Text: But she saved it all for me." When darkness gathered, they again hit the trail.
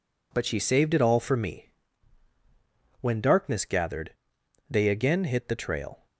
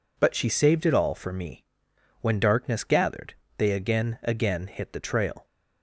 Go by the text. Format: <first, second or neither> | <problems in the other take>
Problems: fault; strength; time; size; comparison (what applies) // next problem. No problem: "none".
first | says "again" twice; at 4.2 s